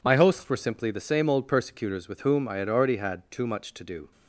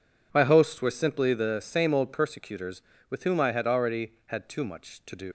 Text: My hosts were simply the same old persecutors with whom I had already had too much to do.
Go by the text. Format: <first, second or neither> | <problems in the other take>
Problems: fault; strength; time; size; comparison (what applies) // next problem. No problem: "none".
first | leaves "do" unfinished; at 5.2 s; 105 ms